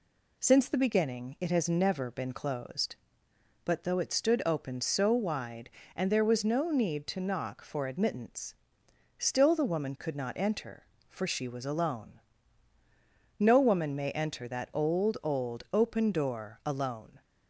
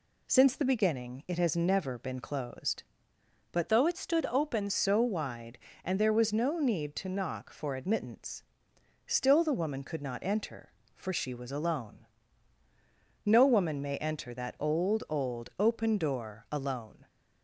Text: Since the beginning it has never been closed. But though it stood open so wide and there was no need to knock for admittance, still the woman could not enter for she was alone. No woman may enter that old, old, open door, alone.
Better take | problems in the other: first | changes voice from "though" to "open"; from 3.6 to 4.7 s; 1.1 s long

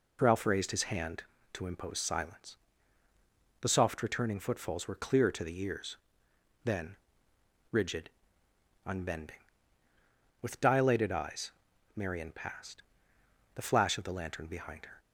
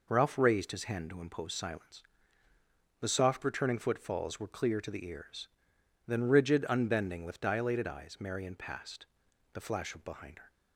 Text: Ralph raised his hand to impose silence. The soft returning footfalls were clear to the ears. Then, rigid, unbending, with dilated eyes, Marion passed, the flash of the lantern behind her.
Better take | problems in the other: first | skips "the lantern"; at 10.0 s

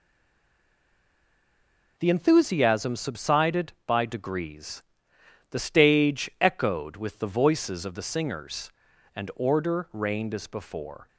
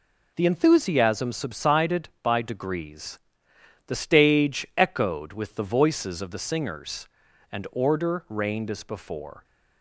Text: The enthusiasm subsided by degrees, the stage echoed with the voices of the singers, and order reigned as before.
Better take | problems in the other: second | stays silent before the first word; noticeable; until 1.9 s; 1.9 s long

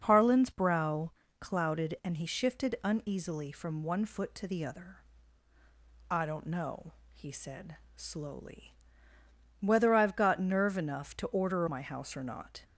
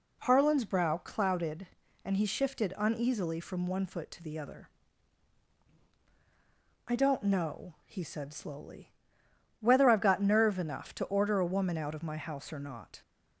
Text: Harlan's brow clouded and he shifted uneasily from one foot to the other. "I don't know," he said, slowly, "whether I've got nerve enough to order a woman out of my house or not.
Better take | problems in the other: second | pauses between "brow" and "clouded"; slight; at 1.1 s; 0.26 s long // skips "a woman out of"; at 11.6 s

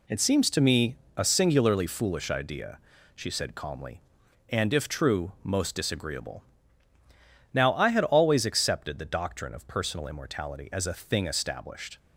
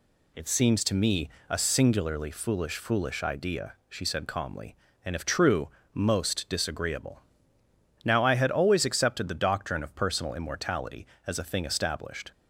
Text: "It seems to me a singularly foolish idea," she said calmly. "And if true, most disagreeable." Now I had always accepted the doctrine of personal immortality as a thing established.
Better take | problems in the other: first | pauses between "me" and "a"; slight; at 1.2 s; 0.20 s long; slight in the first // says "foolish" twice; at 2.7 s

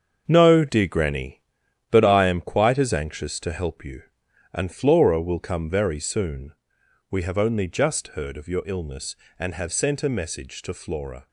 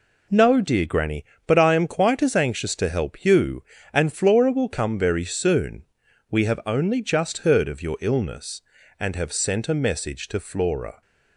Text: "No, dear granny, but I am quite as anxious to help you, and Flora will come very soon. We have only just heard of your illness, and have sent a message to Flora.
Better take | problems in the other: second | gets quieter; strong; throughout; 8.5 dB

